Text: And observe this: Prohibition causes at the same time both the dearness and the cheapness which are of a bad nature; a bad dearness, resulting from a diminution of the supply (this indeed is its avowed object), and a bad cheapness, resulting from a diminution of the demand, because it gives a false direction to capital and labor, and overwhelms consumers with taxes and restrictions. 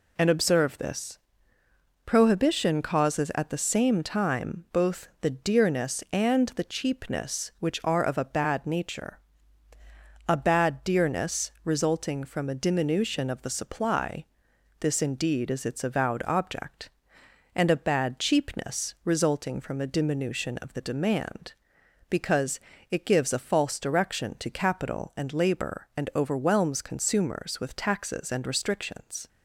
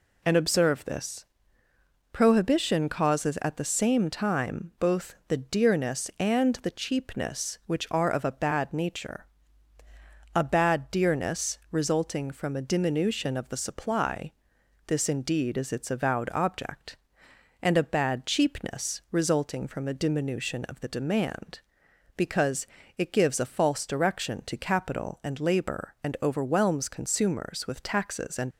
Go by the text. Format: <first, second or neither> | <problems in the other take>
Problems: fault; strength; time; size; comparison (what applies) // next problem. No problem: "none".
first | pauses between "because" and "it"; slight; at 22.6 s; 0.32 s long; slight in the first // stops before "restrictions"; at 28.5 s